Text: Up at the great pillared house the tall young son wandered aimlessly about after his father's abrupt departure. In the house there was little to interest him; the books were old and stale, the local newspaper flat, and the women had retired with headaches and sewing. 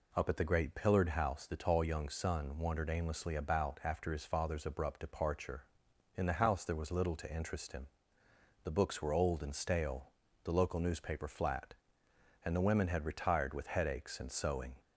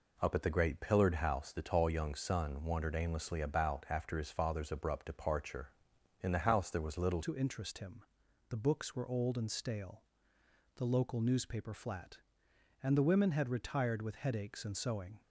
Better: first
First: none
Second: changes voice at "to"; from 7.2 s on; 8.0 s long

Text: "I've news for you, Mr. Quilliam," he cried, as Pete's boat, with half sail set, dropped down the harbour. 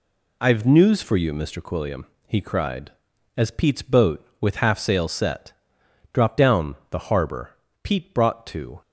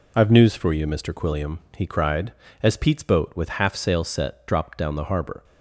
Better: second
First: goes on to say "Pete brought to"; noticeable; from 7.8 s on; 0.98 s long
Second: none

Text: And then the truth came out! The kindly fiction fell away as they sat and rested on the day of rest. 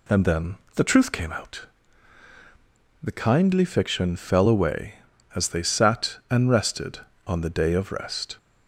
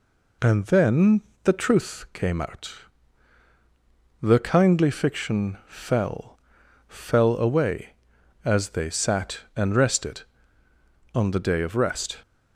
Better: first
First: pauses between "then" and "the"; slight; at 0.5 s; 0.20 s long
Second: pauses between "then" and "the"; slight; at 1.2 s; 0.21 s long // says "fell" twice; at 6.8 s

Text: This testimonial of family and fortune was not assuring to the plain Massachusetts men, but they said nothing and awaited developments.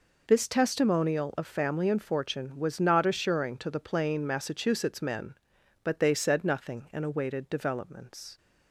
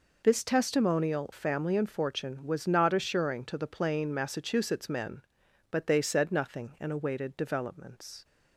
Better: first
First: none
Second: skips "of"; at 1.3 s

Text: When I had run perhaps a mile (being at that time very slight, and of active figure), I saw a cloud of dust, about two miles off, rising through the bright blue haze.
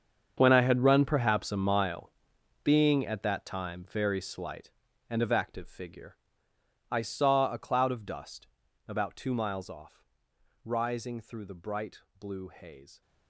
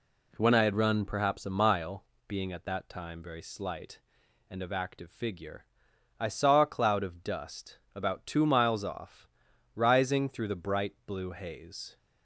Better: second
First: gets quieter; strong; throughout; 15.5 dB // pauses between "bright" and "blue"; slight; at 12.0 s; 0.18 s long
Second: none

